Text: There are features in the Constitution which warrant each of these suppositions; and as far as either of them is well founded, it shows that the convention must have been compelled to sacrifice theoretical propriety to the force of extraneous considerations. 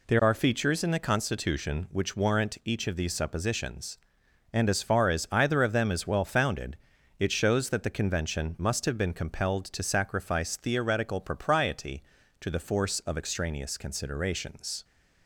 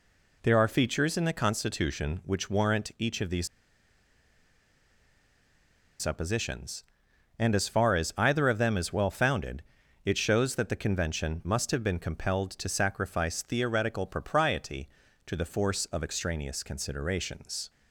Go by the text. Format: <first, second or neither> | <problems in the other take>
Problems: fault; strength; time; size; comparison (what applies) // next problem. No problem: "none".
first | pauses between "these" and "suppositions"; strong; at 3.4 s; 2.5 s long